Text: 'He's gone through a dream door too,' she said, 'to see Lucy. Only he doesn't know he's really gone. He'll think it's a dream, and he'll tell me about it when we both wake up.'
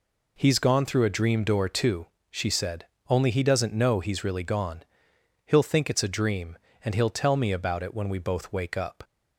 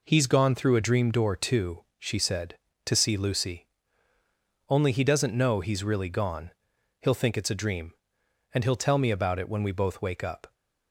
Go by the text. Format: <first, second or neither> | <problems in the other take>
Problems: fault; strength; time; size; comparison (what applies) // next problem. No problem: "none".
second | skips "to see Lucy"; at 2.9 s